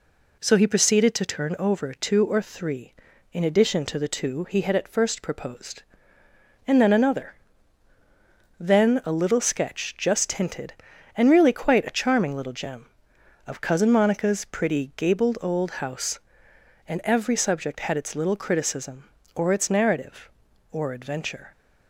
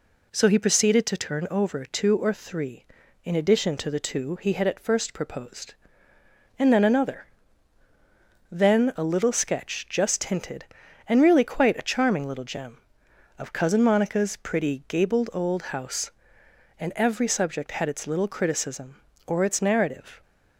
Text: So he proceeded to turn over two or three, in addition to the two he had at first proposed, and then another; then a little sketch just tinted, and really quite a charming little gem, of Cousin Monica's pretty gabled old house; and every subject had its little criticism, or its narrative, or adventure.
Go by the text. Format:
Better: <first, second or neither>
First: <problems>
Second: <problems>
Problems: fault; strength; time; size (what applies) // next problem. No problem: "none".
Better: first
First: none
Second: stops before "or adventure"; at 20.2 s